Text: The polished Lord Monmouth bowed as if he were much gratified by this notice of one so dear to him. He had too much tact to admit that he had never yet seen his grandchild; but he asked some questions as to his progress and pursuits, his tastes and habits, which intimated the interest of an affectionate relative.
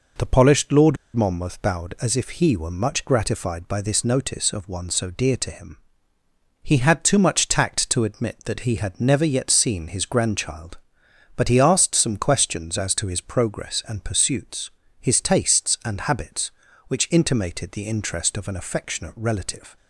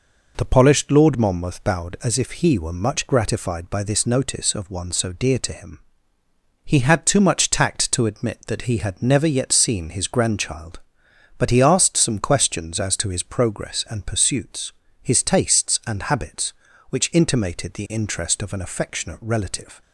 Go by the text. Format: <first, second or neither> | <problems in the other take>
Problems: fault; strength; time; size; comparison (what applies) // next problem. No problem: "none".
second | pauses between "Lord" and "Monmouth"; slight; at 0.9 s; 0.19 s long